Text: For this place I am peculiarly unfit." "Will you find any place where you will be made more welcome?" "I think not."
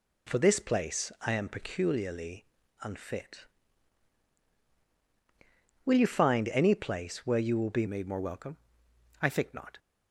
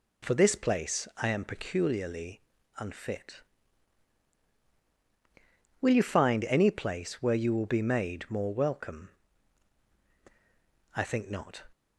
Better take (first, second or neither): second